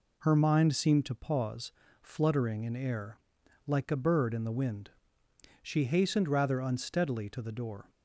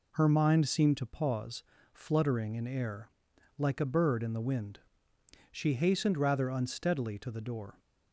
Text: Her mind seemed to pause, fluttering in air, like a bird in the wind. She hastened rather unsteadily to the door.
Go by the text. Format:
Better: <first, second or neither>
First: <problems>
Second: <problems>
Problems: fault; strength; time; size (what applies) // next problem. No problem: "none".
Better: neither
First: none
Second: none